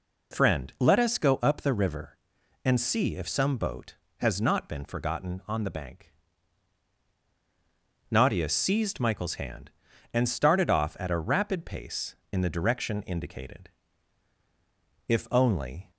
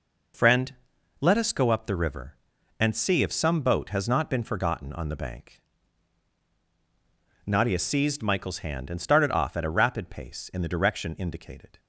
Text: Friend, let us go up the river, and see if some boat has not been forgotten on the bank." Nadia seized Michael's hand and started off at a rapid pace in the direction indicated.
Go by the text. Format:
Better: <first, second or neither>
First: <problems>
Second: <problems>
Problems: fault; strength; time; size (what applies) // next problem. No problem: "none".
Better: second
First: goes on to say "If only"; noticeable; from 15.0 s on; 0.84 s long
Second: none